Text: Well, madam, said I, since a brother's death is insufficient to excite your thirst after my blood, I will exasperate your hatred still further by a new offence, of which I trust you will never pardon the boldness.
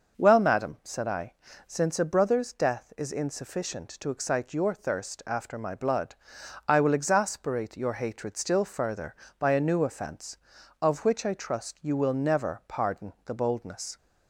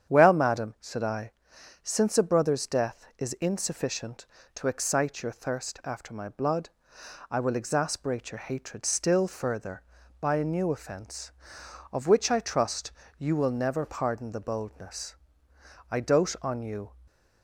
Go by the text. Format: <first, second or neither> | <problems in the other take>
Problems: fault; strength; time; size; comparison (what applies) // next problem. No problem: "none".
first | starts louder than the rest; strong; until 1.1 s; 8.5 dB // pauses between "trust" and "you"; slight; at 12.9 s; 0.28 s long // goes on to say "I dote on you"; noticeable; from 15.9 s on; 0.98 s long